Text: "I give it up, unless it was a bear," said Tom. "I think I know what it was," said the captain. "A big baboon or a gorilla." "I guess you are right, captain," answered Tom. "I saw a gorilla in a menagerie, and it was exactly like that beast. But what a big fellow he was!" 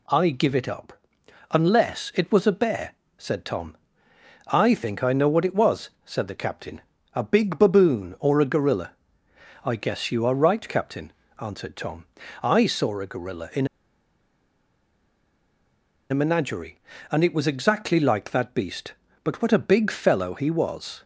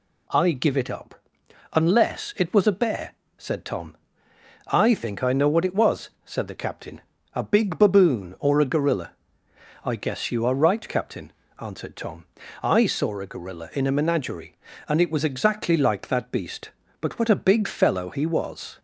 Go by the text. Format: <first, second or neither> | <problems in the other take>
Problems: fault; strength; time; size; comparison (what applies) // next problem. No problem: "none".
second | pauses between "in" and "a"; strong; at 13.6 s; 2.4 s long